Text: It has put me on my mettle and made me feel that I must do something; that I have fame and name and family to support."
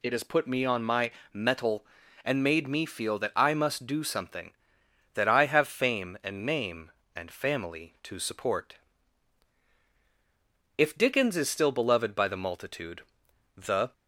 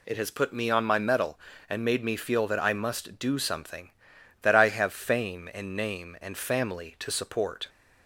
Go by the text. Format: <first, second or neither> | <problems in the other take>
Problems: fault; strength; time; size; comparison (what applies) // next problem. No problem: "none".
second | pauses between "my" and "mettle"; slight; at 1.1 s; 0.22 s long // goes on to say "If Dickens is still beloved by the multitude the"; strong; from 10.7 s on; 3.1 s long